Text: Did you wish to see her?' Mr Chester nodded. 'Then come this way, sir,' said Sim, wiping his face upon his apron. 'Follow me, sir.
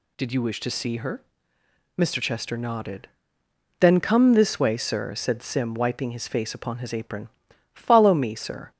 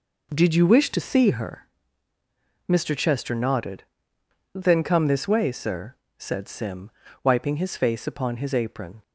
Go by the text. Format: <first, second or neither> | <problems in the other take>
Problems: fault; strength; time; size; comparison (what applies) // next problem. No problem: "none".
first | stops before "Follow me sir"; at 9.0 s